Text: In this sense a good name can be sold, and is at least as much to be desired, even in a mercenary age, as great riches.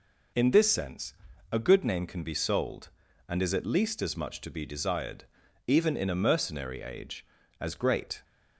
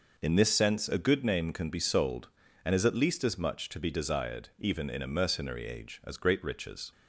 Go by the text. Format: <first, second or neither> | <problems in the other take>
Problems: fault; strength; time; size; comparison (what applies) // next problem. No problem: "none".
second | pauses between "sense" and "a"; at 1.1 s; 0.38 s long // stops before "riches"; at 8.2 s